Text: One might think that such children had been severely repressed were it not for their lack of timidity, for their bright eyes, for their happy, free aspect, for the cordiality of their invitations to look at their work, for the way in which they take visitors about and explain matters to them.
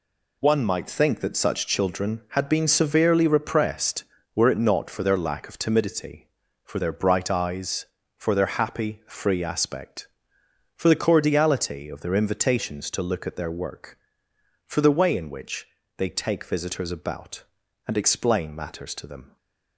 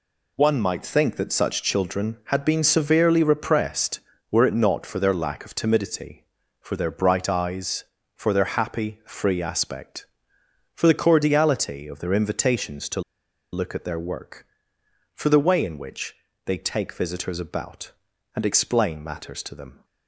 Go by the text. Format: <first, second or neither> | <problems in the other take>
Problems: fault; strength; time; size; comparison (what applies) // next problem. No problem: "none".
first | pauses between "to" and "look"; noticeable; at 13.0 s; 0.51 s long // pauses between "which" and "they"; slight; at 16.1 s; 0.30 s long; slight in the first